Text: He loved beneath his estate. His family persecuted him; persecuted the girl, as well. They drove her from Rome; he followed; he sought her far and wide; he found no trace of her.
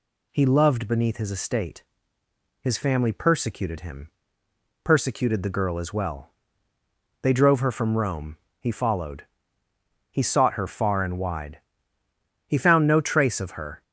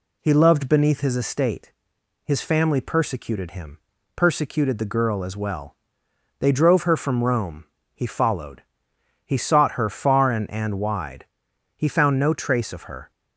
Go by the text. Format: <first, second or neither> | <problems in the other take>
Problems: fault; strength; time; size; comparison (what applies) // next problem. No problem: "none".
first | says "and" twice; at 10.5 s